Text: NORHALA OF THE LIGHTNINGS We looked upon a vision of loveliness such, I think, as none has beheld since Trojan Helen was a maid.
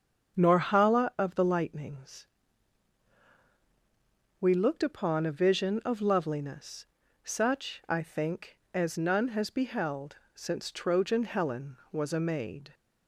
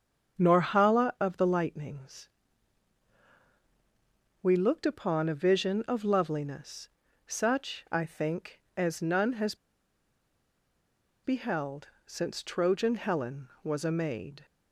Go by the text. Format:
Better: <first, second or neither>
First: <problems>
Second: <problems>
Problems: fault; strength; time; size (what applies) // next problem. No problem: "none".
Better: first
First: starts louder than the rest; strong; until 1.4 s; 7.5 dB // pauses between "LIGHTNINGS" and "We"; strong; at 2.2 s; 2.1 s long // pauses between "loveliness" and "such"; slight; at 6.8 s; 0.36 s long // pauses between "beheld" and "since"; slight; at 10.1 s; 0.18 s long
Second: starts louder than the rest; strong; until 1.4 s; 7.5 dB // pauses between "LIGHTNINGS" and "We"; strong; at 2.2 s; 2.1 s long // pauses between "loveliness" and "such"; slight; at 6.9 s; 0.36 s long // pauses between "has" and "beheld"; strong; at 9.5 s; 1.6 s long // pauses between "beheld" and "since"; slight; at 11.8 s; 0.18 s long